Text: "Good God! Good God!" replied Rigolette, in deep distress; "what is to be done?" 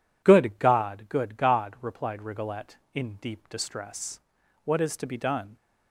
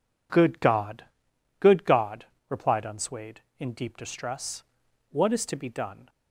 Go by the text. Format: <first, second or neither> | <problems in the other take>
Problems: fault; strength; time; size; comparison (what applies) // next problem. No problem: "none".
first | says "Unswayed" for "Rigolette"; at 2.8 s